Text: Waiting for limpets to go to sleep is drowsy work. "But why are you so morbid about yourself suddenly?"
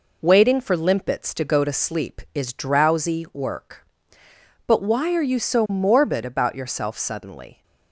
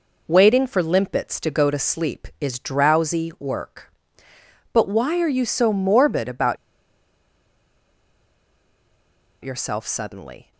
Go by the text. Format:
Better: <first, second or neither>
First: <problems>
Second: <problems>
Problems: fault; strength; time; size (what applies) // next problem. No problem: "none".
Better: first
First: none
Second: pauses between "about" and "yourself"; strong; at 6.5 s; 2.8 s long